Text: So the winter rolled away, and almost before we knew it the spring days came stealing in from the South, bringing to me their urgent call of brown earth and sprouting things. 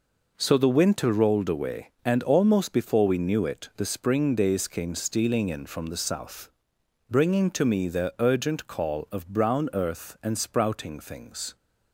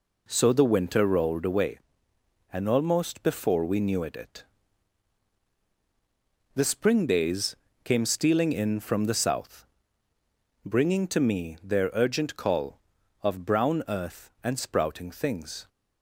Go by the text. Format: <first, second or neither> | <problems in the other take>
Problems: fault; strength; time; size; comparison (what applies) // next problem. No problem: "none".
first | says "it" twice; at 4.1 s // pauses between "days" and "came"; slight; at 7.5 s; 0.30 s long